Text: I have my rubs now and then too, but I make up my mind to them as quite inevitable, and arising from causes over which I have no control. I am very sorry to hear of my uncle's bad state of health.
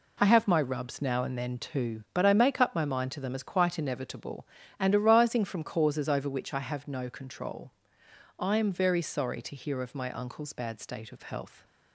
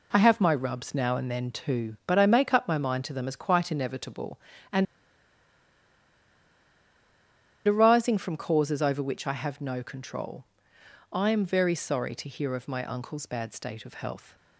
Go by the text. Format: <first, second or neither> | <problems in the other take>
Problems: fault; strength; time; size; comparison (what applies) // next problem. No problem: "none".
first | pauses between "and" and "arising"; strong; at 4.8 s; 2.8 s long